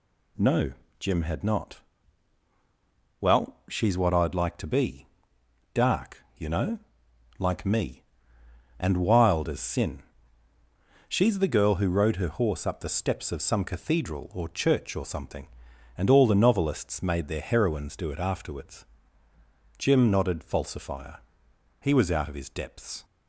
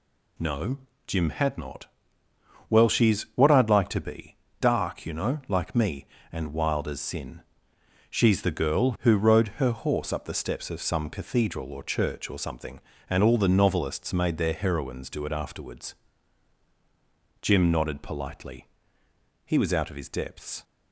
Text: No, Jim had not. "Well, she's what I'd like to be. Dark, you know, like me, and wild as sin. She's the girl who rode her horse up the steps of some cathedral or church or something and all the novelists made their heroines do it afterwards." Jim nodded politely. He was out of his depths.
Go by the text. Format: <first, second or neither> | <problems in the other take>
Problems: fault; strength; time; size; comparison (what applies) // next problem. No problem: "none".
second | says "falsifier" for "politely"; at 20.4 s